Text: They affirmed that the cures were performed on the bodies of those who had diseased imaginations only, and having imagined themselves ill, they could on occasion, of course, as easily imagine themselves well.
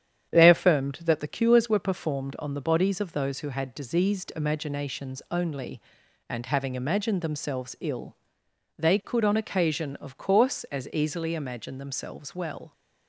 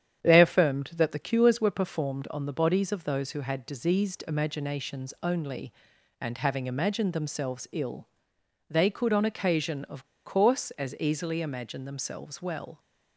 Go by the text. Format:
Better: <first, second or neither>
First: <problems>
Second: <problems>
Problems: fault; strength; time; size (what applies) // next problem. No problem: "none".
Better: first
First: starts louder than the rest; strong; until 1.3 s; 9 dB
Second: starts louder than the rest; strong; until 1.2 s; 9 dB // pauses between "of" and "course"; slight; at 10.0 s; 0.19 s long